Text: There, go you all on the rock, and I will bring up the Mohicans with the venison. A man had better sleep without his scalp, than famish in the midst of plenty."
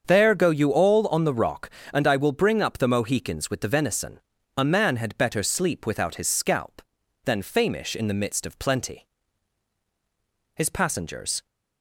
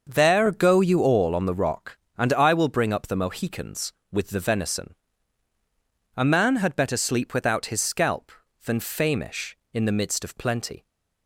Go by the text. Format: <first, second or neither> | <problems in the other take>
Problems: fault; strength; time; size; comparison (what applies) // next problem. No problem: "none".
second | starts louder than the rest; strong; until 1.0 s; 7 dB; also in the second // goes on to say "His passengers"; noticeable; from 10.5 s on; 0.92 s long